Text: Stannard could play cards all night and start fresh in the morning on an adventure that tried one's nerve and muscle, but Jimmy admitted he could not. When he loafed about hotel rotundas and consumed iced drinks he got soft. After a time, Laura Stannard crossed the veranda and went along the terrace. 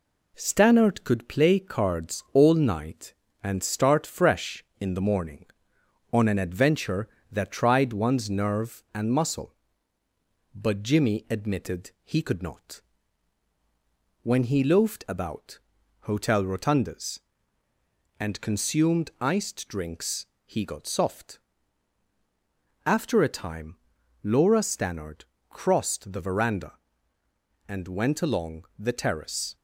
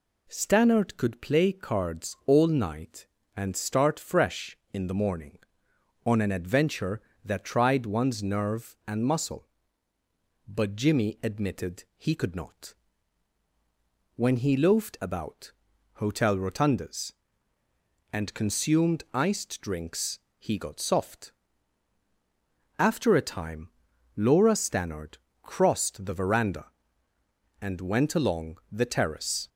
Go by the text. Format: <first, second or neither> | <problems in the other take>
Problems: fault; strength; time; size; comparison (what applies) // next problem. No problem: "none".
second | gets quieter; slight; throughout; 3 dB // pauses between "about" and "hotel"; at 15.5 s; 0.42 s long; also in the second // pauses between "drinks" and "he"; slight; at 20.2 s; 0.20 s long; slight in the second // pauses between "Stannard" and "crossed"; slight; at 25.2 s; 0.26 s long; slight in the second